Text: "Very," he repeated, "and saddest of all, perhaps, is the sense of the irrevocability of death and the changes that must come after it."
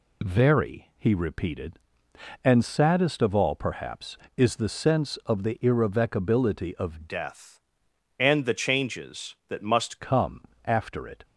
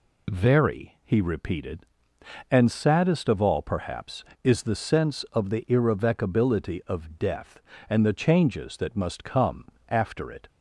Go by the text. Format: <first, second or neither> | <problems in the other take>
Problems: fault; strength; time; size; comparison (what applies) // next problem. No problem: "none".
second | changes voice from "death" to "must"; from 7.0 to 9.9 s; 2.9 s long // pauses between "come" and "after"; slight; at 10.4 s; 0.24 s long; slight in the second